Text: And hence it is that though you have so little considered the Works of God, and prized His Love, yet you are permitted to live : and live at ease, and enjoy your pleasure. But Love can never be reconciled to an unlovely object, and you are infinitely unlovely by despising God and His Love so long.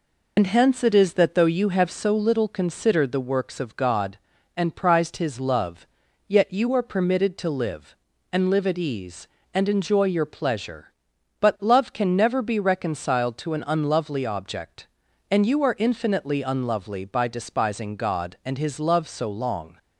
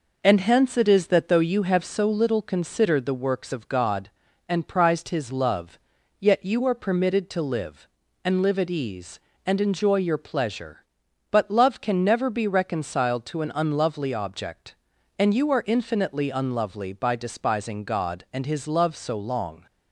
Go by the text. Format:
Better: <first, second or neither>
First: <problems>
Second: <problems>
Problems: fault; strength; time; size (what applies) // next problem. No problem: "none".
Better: second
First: loses the start of "And"; at 0.3 s; 80 ms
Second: none